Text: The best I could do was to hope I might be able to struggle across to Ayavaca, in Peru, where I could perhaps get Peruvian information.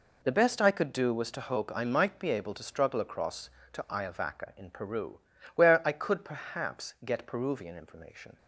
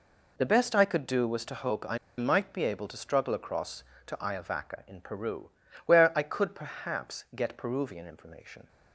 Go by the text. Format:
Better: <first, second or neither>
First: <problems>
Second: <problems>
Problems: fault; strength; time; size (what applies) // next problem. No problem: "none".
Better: first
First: none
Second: pauses between "I" and "might"; slight; at 1.9 s; 0.20 s long